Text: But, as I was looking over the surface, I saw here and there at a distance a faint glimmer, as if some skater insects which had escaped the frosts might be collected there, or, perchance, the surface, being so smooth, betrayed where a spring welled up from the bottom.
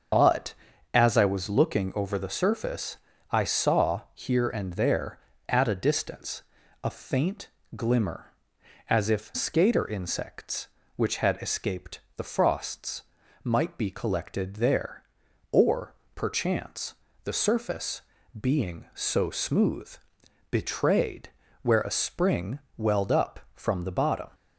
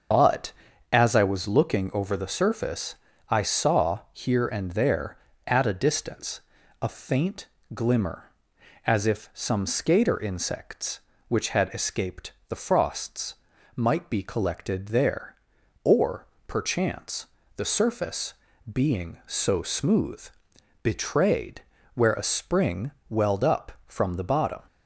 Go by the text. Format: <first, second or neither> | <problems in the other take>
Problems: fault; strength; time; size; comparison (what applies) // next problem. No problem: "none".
second | starts louder than the rest; until 1.5 s; 7 dB; also in the second // pauses between "distance" and "a"; at 6.4 s; 0.40 s long; also in the second // pauses between "faint" and "glimmer"; slight; at 7.4 s; 0.26 s long; slight in the second // skips "some"; at 9.3 s // pauses between "escaped" and "the"; slight; at 12.0 s; 0.16 s long; slight in the second // pauses between "frosts" and "might"; at 13.0 s; 0.42 s long; also in the second // pauses between "betrayed" and "where"; slight; at 21.2 s; 0.34 s long; slight in the second // pauses between "spring" and "welled"; slight; at 22.5 s; 0.18 s long; slight in the second